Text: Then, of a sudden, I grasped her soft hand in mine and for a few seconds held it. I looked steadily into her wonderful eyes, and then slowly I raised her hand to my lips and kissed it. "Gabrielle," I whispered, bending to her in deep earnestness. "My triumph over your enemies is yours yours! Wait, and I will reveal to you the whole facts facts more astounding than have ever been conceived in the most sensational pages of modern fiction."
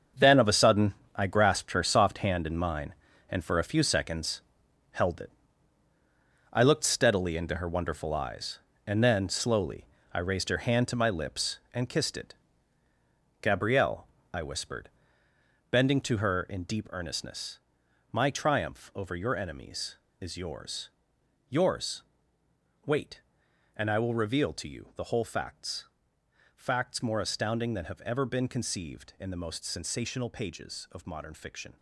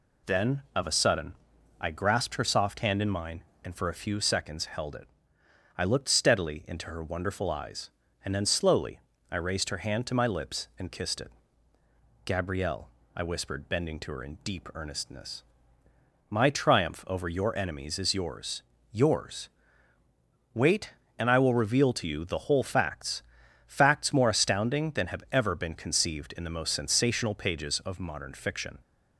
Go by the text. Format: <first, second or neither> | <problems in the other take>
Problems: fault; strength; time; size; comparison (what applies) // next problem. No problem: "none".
second | gets quieter; strong; throughout; 10 dB // pauses between "seconds" and "held"; noticeable; at 4.4 s; 0.50 s long // pauses between "slowly" and "I"; slight; at 9.8 s; 0.26 s long; slight in the second // pauses between "yours" and "yours"; noticeable; at 20.9 s; 0.58 s long; slight in the second // pauses between "facts" and "facts"; noticeable; at 25.8 s; 0.66 s long; also in the second